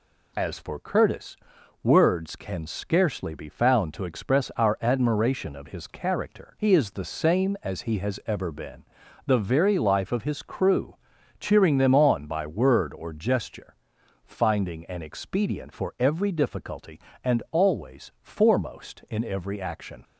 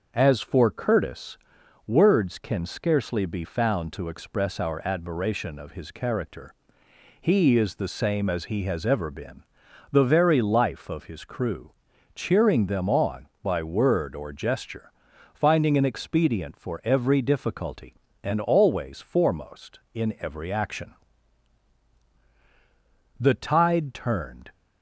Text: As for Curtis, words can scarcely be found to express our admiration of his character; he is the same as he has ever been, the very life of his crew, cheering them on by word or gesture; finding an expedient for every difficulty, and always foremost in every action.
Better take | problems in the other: first | starts louder than the rest; until 1.1 s; 6.5 dB // goes on to say "The tide turned"; from 23.1 s on; 1.3 s long

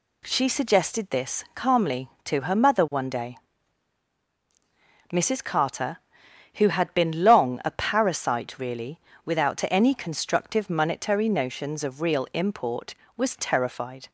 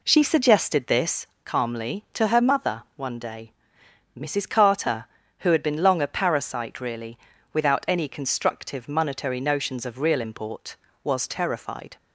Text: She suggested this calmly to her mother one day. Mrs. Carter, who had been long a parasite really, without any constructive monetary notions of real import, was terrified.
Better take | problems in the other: first | starts louder than the rest; slight; until 1.3 s; 3 dB // pauses between "this" and "calmly"; slight; at 1.2 s; 0.16 s long

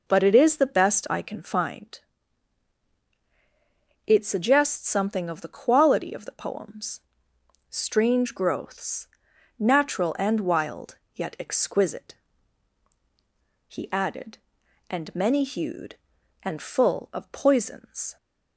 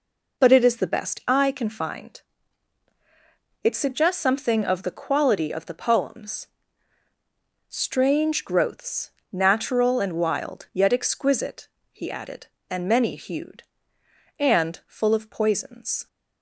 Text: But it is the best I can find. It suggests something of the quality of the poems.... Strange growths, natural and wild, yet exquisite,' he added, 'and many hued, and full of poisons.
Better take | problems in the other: neither | none

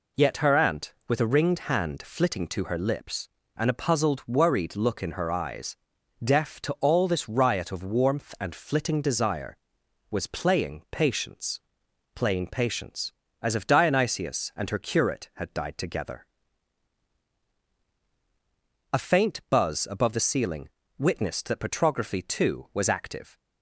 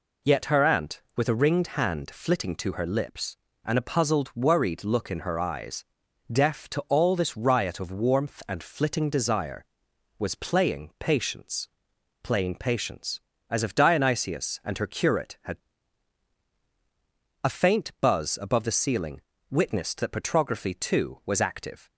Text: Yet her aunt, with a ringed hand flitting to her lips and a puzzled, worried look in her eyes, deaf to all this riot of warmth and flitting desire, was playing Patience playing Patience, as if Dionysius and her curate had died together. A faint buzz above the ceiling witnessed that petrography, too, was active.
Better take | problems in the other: first | pauses between "Patience" and "playing"; noticeable; at 11.6 s; 0.52 s long; noticeable in the first // skips "died together"; at 16.5 s // pauses between "ceiling" and "witnessed"; slight; at 19.2 s; 0.28 s long; slight in the first

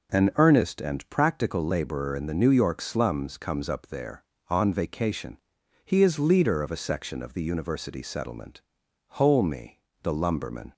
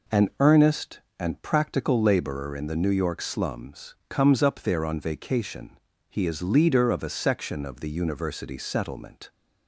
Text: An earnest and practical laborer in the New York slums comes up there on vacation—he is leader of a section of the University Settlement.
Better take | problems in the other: second | goes on to say "Holme the lumberman"; from 9.0 s on; 1.6 s long

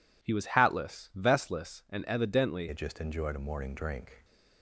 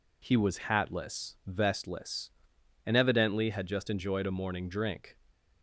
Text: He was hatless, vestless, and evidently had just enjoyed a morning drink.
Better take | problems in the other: second | changes voice at "had"; from 2.6 s on; 1.6 s long

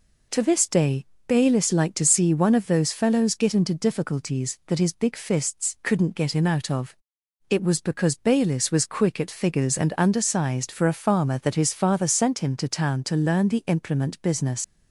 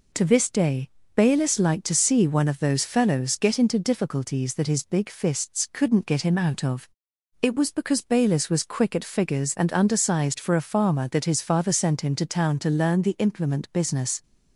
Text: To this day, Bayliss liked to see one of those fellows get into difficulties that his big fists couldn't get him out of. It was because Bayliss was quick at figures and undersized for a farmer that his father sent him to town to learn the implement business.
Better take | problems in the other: second | leaves "business" unfinished; at 14.6 s; 60 ms

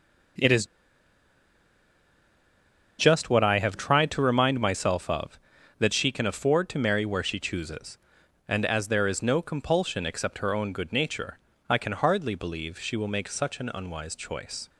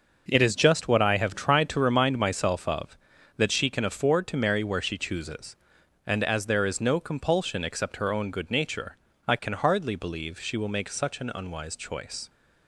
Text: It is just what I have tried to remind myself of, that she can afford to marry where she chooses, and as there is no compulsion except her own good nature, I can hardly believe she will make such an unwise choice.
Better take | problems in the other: second | starts louder than the rest; noticeable; until 3.6 s; 6 dB; noticeable in the second // pauses between "is" and "just"; strong; at 0.6 s; 2.3 s long

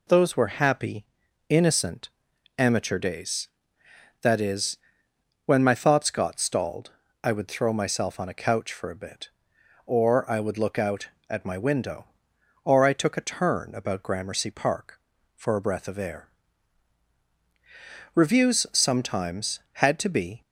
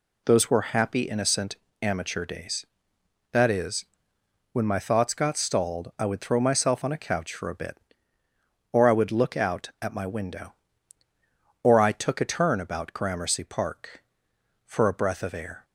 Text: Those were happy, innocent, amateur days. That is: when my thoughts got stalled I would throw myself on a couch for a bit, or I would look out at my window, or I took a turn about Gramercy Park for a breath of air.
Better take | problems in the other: second | pauses between "stalled" and "I"; slight; at 6.9 s; 0.34 s long // goes on to say "Reviews sometimes had to be"; strong; from 18.1 s on; 2.2 s long

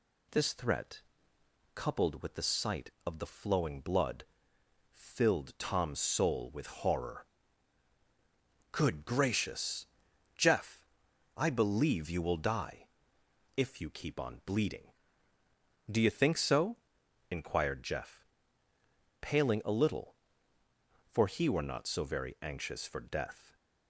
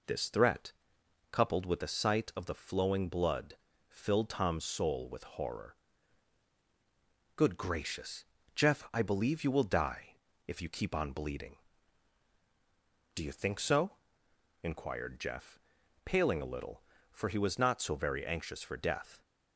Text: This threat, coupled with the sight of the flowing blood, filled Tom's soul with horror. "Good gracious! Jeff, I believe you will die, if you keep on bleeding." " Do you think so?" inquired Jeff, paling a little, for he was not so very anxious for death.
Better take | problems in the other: second | says "were" for "was"; at 21.4 s

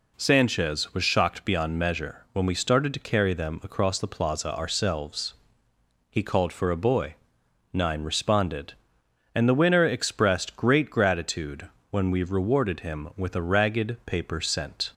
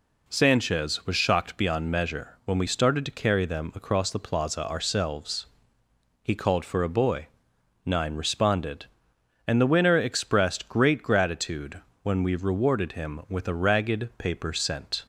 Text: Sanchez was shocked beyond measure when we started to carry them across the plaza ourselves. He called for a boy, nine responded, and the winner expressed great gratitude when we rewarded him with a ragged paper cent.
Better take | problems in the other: neither | pauses between "gratitude" and "when"; slight; the same in both

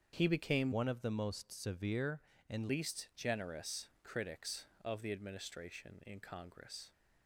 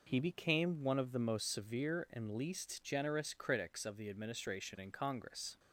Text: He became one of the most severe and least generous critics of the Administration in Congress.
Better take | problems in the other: second | starts louder than the rest; strong; until 1.1 s; 7.5 dB // changes voice from "one" to "and"; from 0.7 to 2.7 s; 2.0 s long // pauses between "generous" and "critics"; slight; at 3.8 s; 0.16 s long

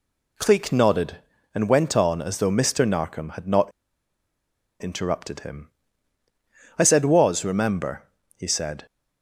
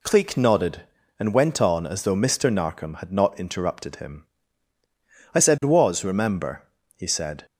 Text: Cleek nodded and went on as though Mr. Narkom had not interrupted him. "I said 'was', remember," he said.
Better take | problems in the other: second | pauses between "not" and "interrupted"; at 3.7 s; 1.1 s long

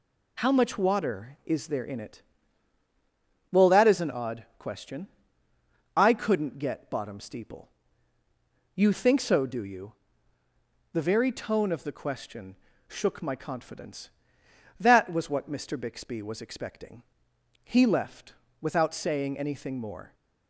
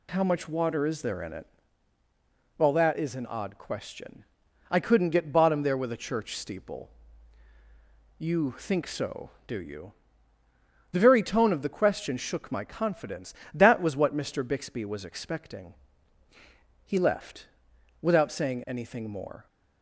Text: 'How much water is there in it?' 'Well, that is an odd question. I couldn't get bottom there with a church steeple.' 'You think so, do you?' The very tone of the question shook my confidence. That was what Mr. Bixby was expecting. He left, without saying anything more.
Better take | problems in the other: second | skips "there with a church"; at 7.1 s // pauses between "question" and "shook"; slight; at 12.5 s; 0.32 s long

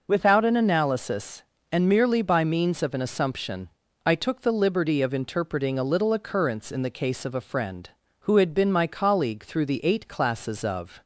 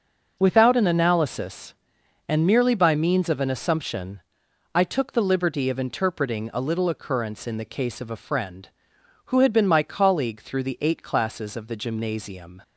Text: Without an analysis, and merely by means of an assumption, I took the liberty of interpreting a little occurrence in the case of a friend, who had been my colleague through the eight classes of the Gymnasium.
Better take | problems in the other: second | stops before "the Gymnasium"; at 11.0 s

